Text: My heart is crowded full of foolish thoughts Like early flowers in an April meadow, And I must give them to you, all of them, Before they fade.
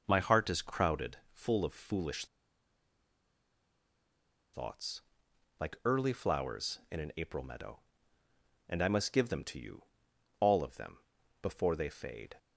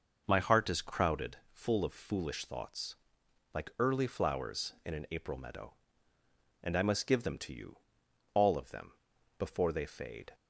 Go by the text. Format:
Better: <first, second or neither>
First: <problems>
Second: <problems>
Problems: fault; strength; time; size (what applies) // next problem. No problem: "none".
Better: second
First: pauses between "crowded" and "full"; slight; at 1.1 s; 0.16 s long // pauses between "foolish" and "thoughts"; strong; at 2.2 s; 2.2 s long // pauses between "thoughts" and "Like"; noticeable; at 4.9 s; 0.60 s long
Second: pauses between "crowded" and "full"; slight; at 1.3 s; 0.16 s long // pauses between "thoughts" and "Like"; noticeable; at 2.9 s; 0.60 s long